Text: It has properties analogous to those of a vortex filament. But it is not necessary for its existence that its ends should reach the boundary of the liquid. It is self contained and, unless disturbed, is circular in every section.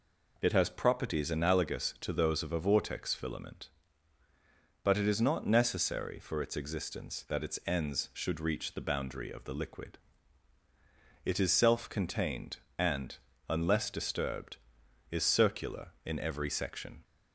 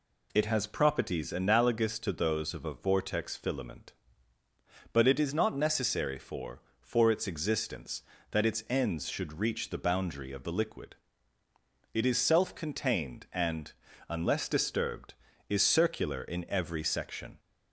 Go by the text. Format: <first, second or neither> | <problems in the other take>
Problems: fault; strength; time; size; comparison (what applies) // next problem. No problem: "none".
first | says "for" twice; at 6.8 s